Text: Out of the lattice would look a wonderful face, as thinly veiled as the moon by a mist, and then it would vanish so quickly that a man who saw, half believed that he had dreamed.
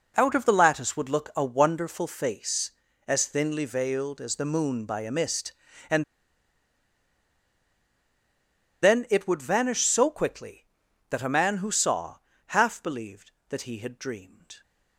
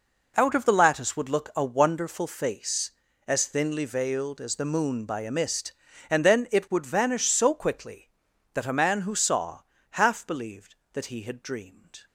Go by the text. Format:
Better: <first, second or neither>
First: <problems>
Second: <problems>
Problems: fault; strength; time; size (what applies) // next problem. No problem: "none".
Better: second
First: pauses between "and" and "then"; strong; at 6.0 s; 2.7 s long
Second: none